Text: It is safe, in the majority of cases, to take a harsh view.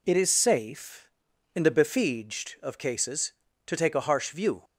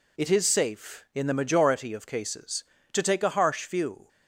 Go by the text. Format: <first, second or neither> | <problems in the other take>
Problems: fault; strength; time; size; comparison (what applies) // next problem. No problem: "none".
second | says "befieged" for "majority"; at 1.6 s